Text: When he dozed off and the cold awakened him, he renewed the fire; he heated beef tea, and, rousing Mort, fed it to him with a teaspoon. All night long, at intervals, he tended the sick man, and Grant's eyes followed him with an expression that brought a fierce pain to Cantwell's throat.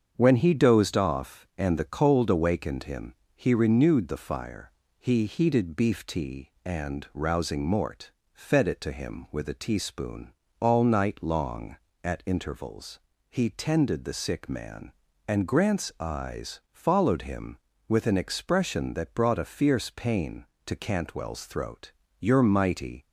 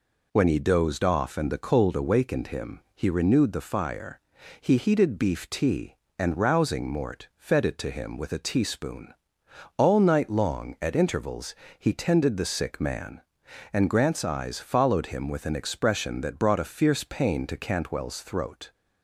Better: second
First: starts louder than the rest; strong; until 1.1 s; 7 dB // goes on to say "You're mighty"; noticeable; from 22.1 s on; 0.86 s long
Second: none

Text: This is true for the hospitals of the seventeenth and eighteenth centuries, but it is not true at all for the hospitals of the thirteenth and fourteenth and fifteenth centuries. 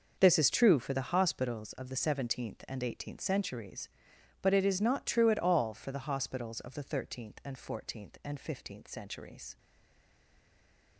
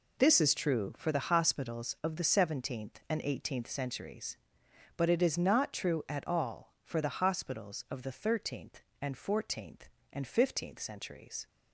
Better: second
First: starts louder than the rest; noticeable; until 1.2 s; 6 dB // stays silent after the last word; noticeable; from 9.5 s on; 1.4 s long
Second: none

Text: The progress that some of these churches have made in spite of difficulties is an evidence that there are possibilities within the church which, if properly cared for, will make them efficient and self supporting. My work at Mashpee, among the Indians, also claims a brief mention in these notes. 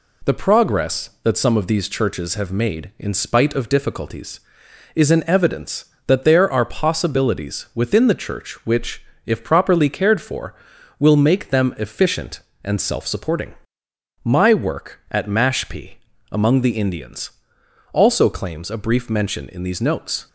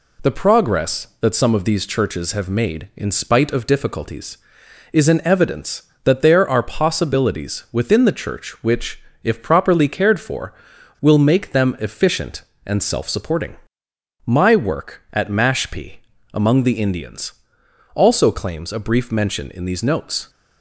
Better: neither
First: none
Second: none

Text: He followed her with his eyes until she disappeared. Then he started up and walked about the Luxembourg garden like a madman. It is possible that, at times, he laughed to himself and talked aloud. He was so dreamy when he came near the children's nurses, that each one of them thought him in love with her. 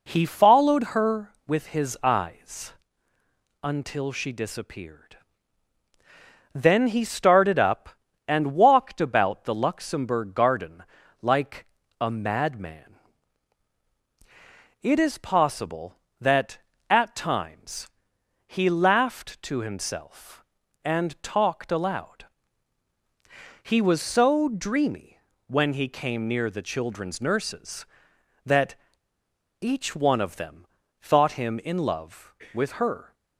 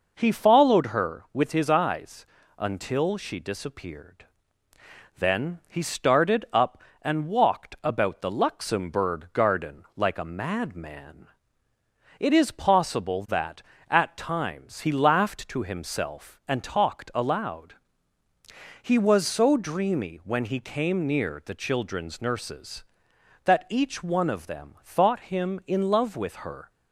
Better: second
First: pauses between "eyes" and "until"; noticeable; at 2.7 s; 0.90 s long // pauses between "garden" and "like"; at 10.8 s; 0.38 s long // pauses between "like" and "a"; slight; at 11.6 s; 0.34 s long // pauses between "dreamy" and "when"; slight; at 25.1 s; 0.28 s long // pauses between "that" and "each"; noticeable; at 28.7 s; 0.84 s long // pauses between "them" and "thought"; slight; at 30.6 s; 0.34 s long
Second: pauses between "eyes" and "until"; slight; at 2.2 s; 0.32 s long

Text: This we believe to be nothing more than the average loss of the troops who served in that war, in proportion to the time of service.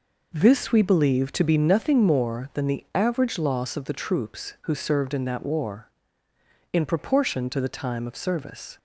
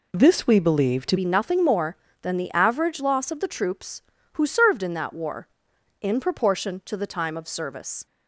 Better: first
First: none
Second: changes voice at "be"; from 1.1 s on; 6.9 s long

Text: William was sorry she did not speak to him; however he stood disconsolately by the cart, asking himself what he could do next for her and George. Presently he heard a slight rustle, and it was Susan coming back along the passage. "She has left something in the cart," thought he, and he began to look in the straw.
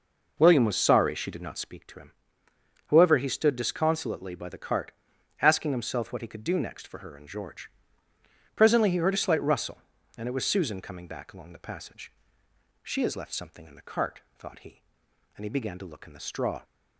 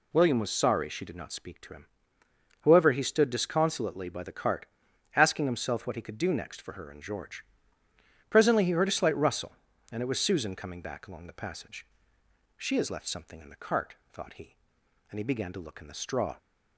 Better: second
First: starts louder than the rest; noticeable; until 1.7 s; 5 dB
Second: none

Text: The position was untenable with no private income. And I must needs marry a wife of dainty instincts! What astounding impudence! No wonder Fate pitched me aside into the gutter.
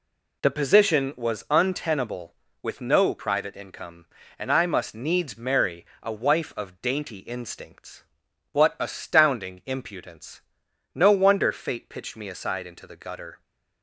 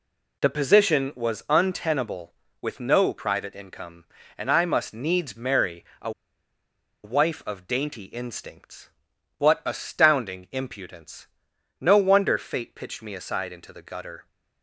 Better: first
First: pauses between "marry" and "a"; slight; at 5.8 s; 0.16 s long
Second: pauses between "marry" and "a"; slight; at 5.8 s; 0.16 s long // pauses between "a" and "wife"; noticeable; at 6.1 s; 0.93 s long

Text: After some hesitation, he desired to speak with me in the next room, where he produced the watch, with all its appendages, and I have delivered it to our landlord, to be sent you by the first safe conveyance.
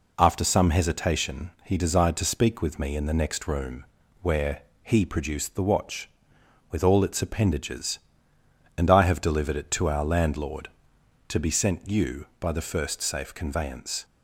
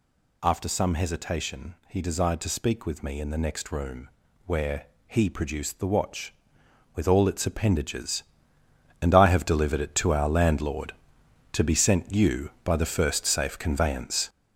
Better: first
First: pauses between "where" and "he"; slight; at 4.6 s; 0.22 s long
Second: gets louder; throughout; 6.5 dB // pauses between "where" and "he"; slight; at 4.8 s; 0.22 s long

